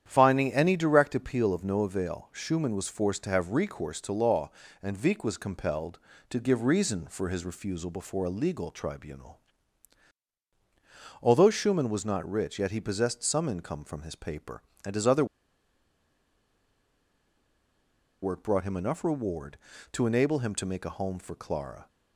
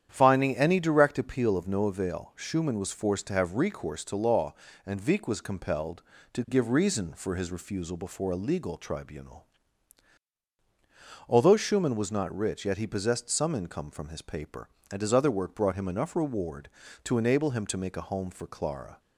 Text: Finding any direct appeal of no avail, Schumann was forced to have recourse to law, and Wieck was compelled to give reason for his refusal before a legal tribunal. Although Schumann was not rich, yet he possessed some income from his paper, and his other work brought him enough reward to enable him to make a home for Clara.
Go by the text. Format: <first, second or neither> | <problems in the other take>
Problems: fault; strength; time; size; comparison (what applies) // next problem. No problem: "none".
second | starts louder than the rest; strong; until 1.0 s; 9.5 dB; strong in the second // pauses between "other" and "work"; strong; at 15.2 s; 2.9 s long